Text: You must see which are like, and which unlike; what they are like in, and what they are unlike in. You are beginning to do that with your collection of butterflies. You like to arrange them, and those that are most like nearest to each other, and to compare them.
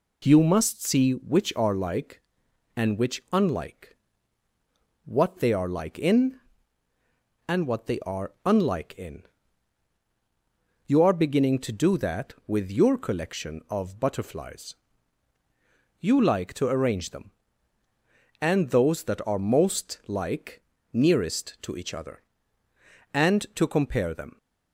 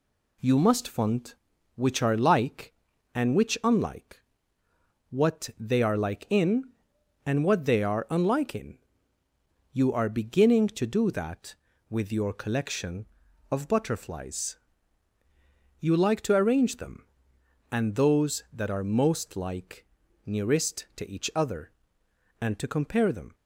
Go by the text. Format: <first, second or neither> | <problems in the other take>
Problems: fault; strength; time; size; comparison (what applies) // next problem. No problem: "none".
first | says "font" for "see"; at 0.8 s // pauses between "like" and "nearest"; at 19.8 s; 0.38 s long; slight in the first